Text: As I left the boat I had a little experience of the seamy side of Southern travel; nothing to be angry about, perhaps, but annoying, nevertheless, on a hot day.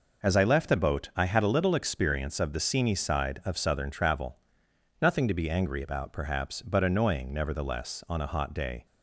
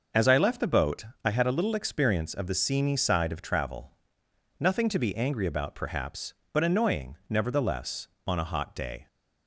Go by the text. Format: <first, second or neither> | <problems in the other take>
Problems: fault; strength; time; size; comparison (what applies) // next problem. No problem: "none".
first | starts louder than the rest; noticeable; until 1.3 s; 6 dB // pauses between "boat" and "I"; slight; at 1.0 s; 0.20 s long // skips "Southern"; at 3.4 s